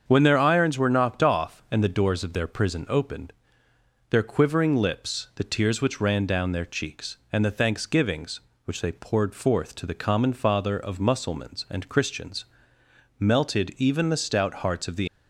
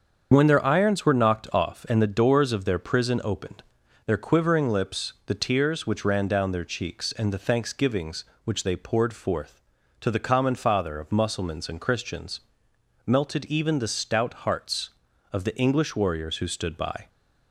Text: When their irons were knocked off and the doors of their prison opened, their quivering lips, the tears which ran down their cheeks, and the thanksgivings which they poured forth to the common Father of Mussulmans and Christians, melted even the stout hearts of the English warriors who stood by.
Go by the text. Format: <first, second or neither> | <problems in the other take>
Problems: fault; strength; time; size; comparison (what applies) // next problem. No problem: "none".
second | starts louder than the rest; strong; until 1.0 s; 7 dB; also in the second // stops before "English warriors who stood by"; at 15.0 s